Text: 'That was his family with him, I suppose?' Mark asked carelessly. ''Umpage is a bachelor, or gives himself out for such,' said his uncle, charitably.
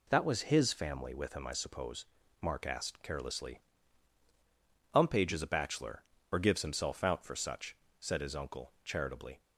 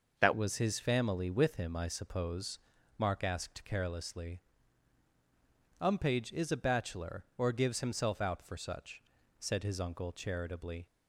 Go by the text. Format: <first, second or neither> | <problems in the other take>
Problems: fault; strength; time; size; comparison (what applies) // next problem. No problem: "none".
first | changes voice at "was"; from 0.3 s on; 10.5 s long